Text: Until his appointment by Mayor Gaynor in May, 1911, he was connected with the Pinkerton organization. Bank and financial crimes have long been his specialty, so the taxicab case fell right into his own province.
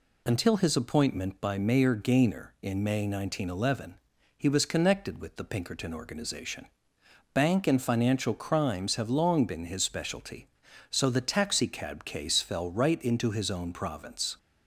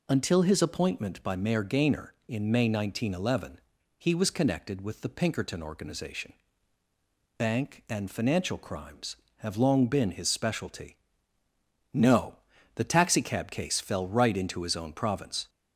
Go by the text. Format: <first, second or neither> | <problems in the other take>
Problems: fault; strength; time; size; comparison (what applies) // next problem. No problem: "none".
first | says "no" for "so"; at 11.9 s